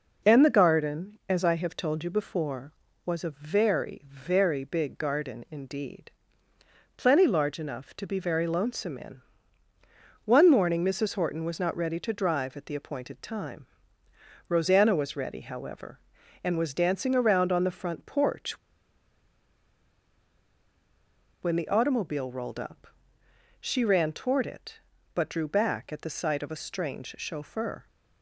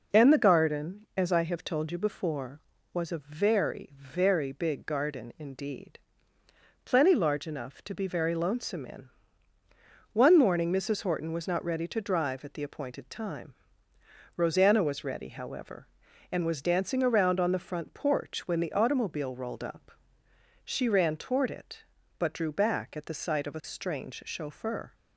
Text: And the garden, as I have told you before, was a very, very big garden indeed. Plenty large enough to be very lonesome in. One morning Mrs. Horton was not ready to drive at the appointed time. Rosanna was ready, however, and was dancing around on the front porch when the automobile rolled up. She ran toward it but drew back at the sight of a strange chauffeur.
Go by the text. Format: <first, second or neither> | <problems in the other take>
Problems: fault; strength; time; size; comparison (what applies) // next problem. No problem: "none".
second | pauses between "porch" and "when"; strong; at 18.5 s; 2.8 s long